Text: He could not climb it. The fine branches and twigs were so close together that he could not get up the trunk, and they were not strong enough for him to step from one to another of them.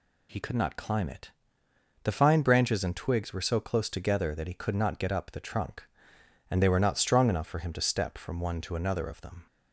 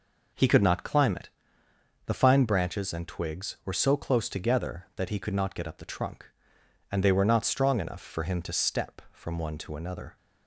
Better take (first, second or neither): first